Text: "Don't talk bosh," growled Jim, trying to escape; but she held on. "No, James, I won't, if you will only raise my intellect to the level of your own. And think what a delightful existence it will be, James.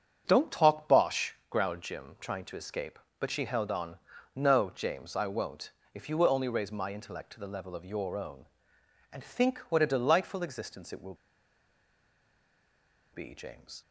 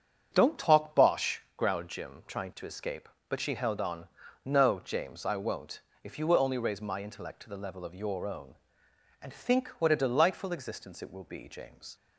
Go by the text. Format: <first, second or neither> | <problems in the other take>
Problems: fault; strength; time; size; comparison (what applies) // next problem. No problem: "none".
second | starts louder than the rest; strong; until 1.2 s; 7.5 dB; strong in the second // pauses between "will" and "be"; strong; at 11.1 s; 1.9 s long